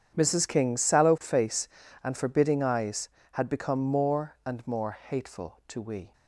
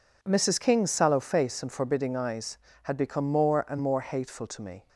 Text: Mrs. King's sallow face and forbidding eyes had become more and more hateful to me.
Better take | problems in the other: second | starts louder than the rest; strong; until 1.1 s; 9 dB // says "we" for "me"; at 5.8 s

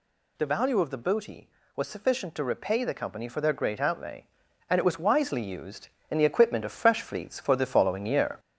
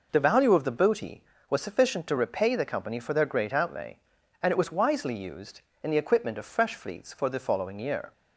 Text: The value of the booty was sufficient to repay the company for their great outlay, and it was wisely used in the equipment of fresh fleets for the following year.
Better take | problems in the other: second | gets louder; slight; throughout; 3 dB

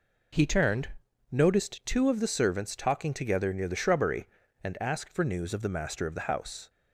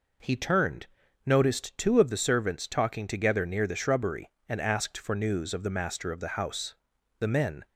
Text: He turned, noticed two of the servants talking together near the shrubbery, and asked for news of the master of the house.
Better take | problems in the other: first | goes on to say "The men"; slight; from 7.1 s on; 0.48 s long

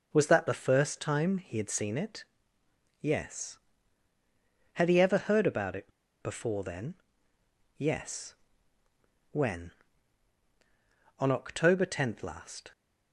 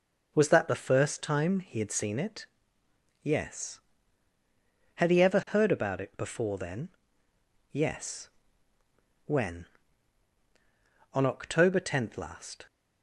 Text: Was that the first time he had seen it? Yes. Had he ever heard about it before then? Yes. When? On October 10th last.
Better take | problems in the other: second | pauses between "it" and "before"; slight; at 5.9 s; 0.31 s long

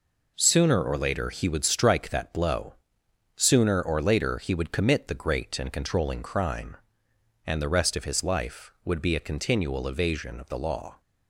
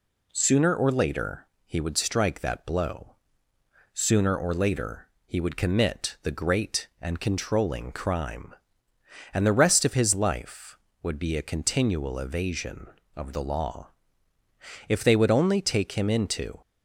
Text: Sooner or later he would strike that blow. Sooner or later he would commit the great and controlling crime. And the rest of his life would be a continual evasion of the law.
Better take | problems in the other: first | pauses between "later" and "he"; slight; at 1.4 s; 0.18 s long // pauses between "later" and "he"; slight; at 5.0 s; 0.18 s long // goes on to say "If they would only take him into"; strong; from 14.8 s on; 1.7 s long

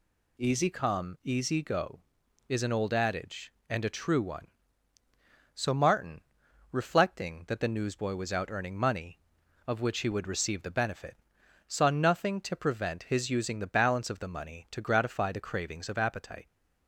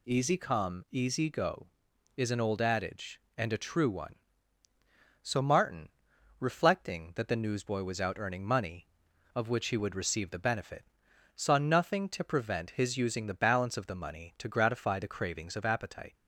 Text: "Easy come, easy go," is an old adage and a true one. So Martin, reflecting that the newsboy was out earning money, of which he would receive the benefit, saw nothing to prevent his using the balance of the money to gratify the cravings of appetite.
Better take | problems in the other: neither | none

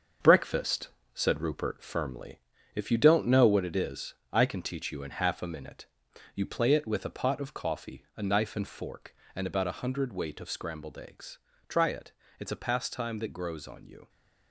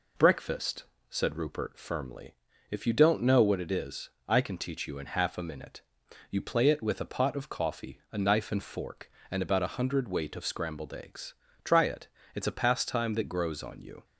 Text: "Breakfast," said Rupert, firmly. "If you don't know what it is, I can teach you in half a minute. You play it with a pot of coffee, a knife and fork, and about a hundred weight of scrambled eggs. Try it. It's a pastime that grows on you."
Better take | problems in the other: second | gets quieter; strong; throughout; 7.5 dB

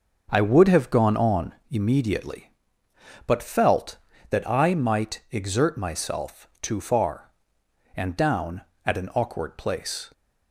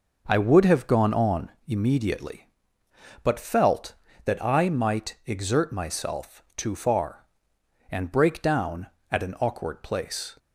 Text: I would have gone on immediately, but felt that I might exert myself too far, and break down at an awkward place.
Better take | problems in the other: second | pauses between "on" and "immediately"; slight; at 1.5 s; 0.16 s long; slight in the second // skips "break"; at 8.1 s

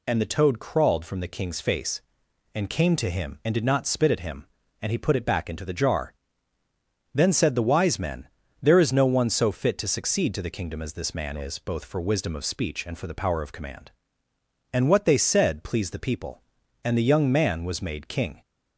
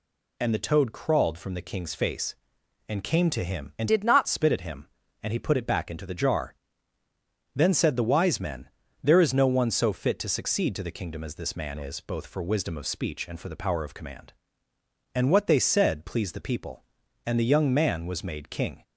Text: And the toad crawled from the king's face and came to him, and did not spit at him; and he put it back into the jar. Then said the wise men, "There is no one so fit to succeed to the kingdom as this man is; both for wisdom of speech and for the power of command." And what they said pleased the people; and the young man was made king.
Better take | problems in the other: first | changes voice from "did" to "not"; from 3.8 to 4.2 s; 0.4 s long

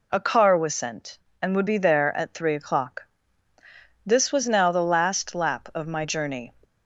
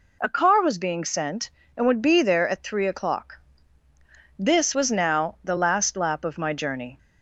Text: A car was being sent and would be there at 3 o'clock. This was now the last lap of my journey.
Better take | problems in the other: second | skips "being"; at 0.7 s

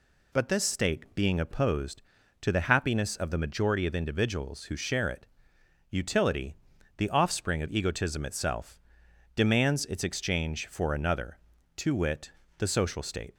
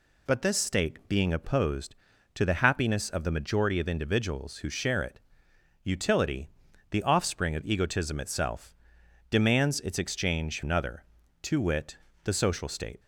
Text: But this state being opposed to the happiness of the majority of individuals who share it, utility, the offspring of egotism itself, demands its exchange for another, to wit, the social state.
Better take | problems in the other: first | skips "for"; at 10.6 s

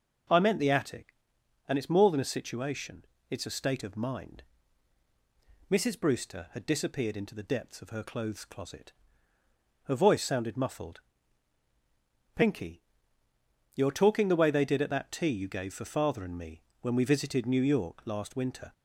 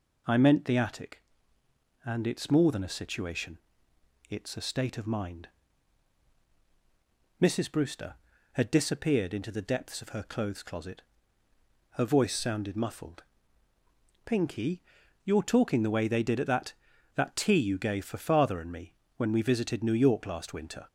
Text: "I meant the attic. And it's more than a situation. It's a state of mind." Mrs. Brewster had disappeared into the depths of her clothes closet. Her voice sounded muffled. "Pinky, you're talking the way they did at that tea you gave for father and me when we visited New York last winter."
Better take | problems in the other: first | says "that" twice; at 17.1 s // pauses between "me" and "when"; slight; at 18.9 s; 0.24 s long; slight in the first

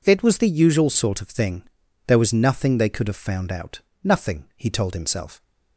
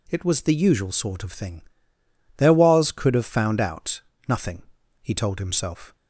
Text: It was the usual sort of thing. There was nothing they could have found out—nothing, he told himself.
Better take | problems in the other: first | skips "nothing they"; at 2.9 s

